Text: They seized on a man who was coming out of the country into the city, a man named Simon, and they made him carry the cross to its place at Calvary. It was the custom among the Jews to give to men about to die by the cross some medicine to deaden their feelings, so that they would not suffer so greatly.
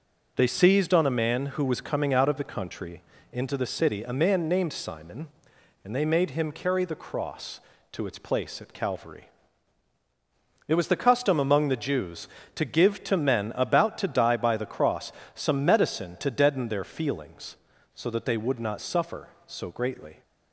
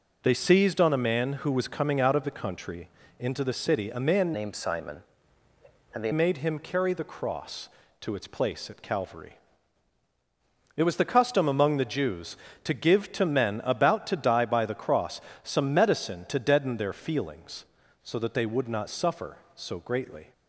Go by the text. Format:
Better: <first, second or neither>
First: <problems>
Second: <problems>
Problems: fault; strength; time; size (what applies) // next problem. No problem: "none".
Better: first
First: pauses between "country" and "into"; slight; at 3.0 s; 0.30 s long // pauses between "cross" and "some"; slight; at 15.1 s; 0.22 s long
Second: pauses between "country" and "into"; slight; at 2.8 s; 0.30 s long // changes voice from "named" to "they"; from 4.3 to 6.1 s; 1.8 s long // pauses between "cross" and "some"; slight; at 15.2 s; 0.22 s long